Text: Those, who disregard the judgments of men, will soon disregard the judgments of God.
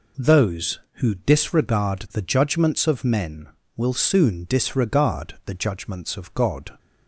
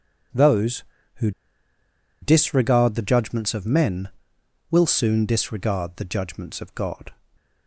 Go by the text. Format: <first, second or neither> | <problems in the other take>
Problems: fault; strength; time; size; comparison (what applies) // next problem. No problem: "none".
first | pauses between "who" and "disregard"; noticeable; at 1.3 s; 0.90 s long // stays silent after the last word; slight; from 7.1 s on; 0.5 s long